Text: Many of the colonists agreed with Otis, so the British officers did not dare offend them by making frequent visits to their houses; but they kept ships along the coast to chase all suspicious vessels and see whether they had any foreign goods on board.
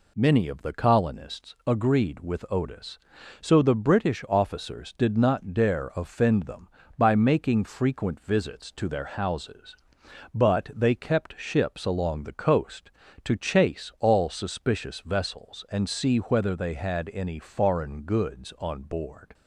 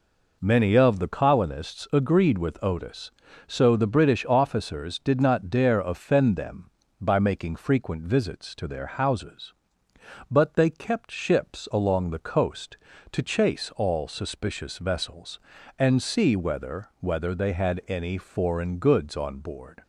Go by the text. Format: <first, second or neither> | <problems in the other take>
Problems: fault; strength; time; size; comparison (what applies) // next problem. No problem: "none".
first | says "whether" twice; at 17.0 s